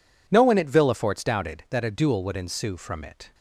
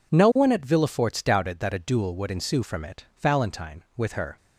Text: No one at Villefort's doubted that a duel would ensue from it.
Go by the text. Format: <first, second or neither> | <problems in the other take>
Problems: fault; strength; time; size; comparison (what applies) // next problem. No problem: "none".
first | goes on to say "Valentine with her"; noticeable; from 3.2 s on; 1.1 s long